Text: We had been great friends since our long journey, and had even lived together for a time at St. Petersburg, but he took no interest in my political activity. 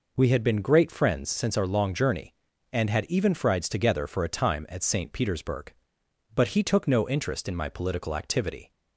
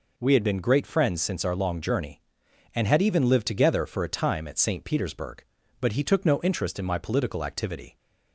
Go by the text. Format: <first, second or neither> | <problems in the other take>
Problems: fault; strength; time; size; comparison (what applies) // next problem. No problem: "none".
second | says "frieds" for "lived"; at 3.3 s